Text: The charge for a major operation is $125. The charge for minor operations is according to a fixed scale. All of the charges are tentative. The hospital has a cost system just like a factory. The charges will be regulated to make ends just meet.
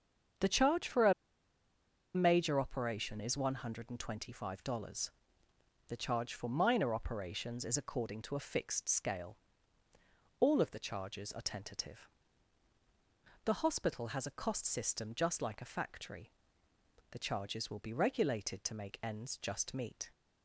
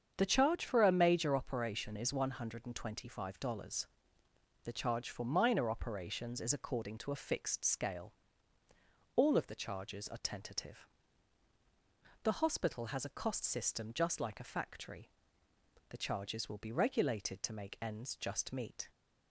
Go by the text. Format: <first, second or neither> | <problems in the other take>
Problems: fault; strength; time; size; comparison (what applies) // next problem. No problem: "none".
second | starts louder than the rest; strong; until 2.4 s; 7.5 dB; strong in the second // pauses between "a" and "major"; at 1.1 s; 1.0 s long